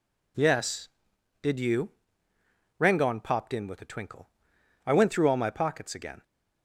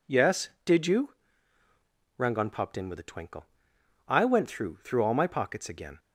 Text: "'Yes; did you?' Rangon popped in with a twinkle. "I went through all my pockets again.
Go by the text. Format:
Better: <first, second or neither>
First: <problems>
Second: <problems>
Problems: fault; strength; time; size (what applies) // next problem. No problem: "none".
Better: first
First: none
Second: says "through" twice; at 4.7 s